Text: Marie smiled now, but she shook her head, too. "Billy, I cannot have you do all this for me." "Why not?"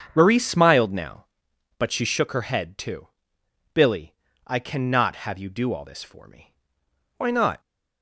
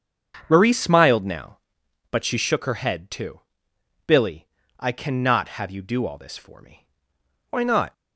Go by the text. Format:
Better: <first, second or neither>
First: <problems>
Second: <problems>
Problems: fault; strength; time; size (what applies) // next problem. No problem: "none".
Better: neither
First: starts louder than the rest; strong; until 1.1 s; 7 dB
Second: starts louder than the rest; until 1.5 s; 7 dB